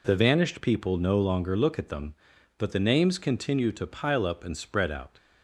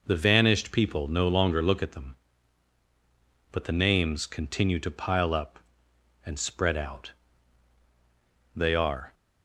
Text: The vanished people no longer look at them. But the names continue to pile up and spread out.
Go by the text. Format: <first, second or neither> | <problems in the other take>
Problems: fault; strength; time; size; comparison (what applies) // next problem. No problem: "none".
first | goes on to say "They are"; from 8.5 s on; 0.58 s long